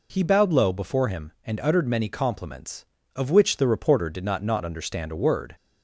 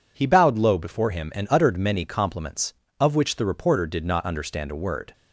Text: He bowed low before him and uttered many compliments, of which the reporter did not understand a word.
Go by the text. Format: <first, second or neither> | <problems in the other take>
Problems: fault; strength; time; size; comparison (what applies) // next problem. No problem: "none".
second | says "not" twice; at 4.4 s